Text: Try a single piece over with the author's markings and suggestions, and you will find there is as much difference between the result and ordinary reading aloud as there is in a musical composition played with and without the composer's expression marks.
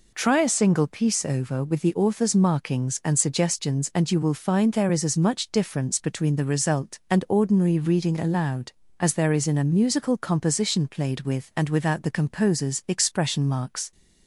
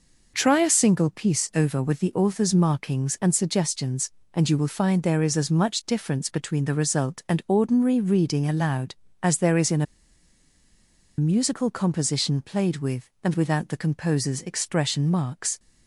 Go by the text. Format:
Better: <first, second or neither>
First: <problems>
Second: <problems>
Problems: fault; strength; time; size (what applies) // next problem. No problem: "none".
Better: first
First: none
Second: pauses between "a" and "musical"; strong; at 9.8 s; 1.3 s long